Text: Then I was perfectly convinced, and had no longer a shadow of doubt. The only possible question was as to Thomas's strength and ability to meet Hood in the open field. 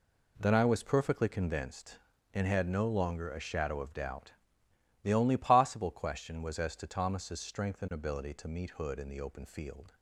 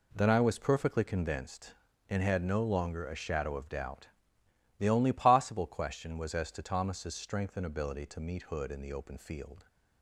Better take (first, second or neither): neither